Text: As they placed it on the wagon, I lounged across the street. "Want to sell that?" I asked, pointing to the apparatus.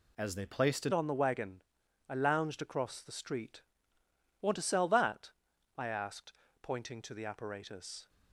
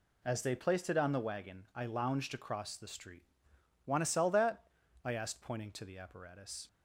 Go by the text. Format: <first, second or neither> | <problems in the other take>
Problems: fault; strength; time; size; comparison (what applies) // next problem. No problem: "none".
second | changes voice at "on"; from 0.9 s on; 7.1 s long